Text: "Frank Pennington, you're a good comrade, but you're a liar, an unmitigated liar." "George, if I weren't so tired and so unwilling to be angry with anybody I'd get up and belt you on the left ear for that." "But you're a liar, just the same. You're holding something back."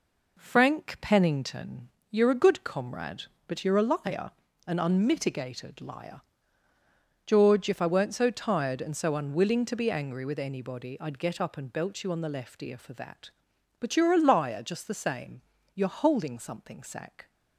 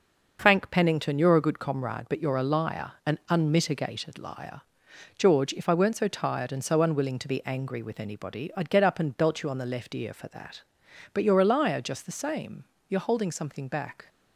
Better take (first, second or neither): second